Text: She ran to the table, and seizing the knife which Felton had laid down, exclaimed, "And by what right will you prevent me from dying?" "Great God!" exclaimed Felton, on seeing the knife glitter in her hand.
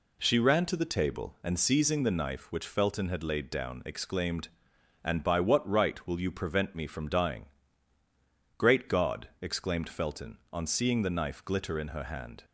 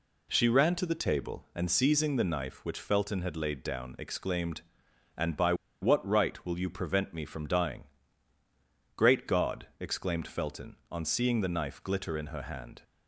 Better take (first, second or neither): first